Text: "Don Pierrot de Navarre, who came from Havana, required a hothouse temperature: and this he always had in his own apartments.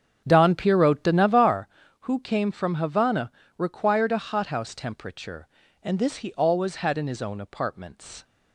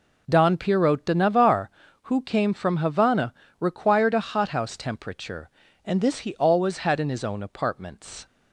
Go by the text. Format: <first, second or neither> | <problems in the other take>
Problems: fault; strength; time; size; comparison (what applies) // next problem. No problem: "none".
second | starts louder than the rest; strong; until 1.5 s; 8 dB